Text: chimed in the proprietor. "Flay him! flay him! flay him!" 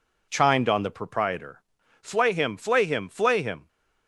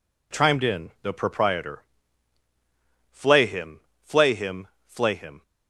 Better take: second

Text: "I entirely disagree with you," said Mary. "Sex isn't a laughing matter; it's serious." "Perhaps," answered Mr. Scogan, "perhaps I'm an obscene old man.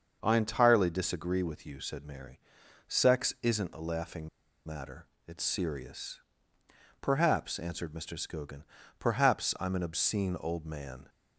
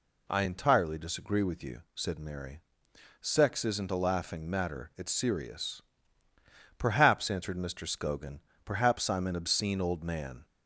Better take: second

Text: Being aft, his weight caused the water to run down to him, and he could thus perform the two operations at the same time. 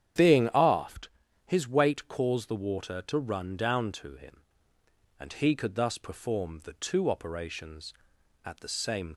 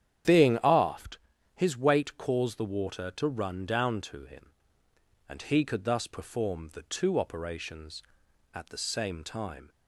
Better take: second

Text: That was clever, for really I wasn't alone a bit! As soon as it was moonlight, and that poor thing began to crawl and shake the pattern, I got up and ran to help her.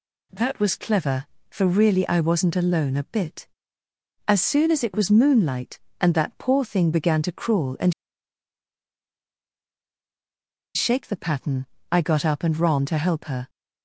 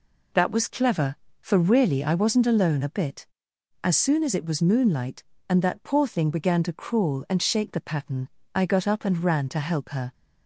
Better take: second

